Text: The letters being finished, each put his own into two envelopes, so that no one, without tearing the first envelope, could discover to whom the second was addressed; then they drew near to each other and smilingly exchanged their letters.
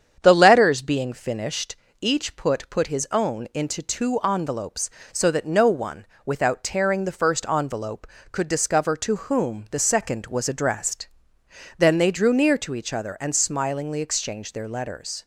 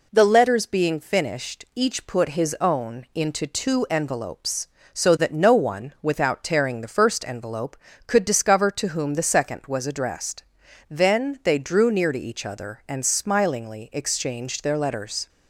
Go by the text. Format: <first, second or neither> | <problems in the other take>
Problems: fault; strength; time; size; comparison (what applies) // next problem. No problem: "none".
second | starts louder than the rest; strong; until 1.2 s; 8 dB // says "put" twice; at 2.6 s